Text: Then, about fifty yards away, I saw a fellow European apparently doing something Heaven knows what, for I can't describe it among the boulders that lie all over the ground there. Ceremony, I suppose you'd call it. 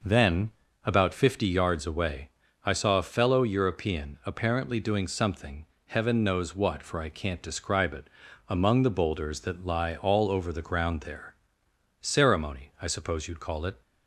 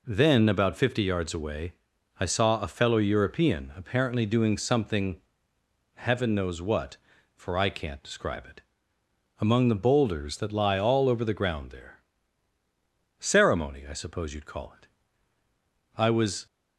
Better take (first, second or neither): first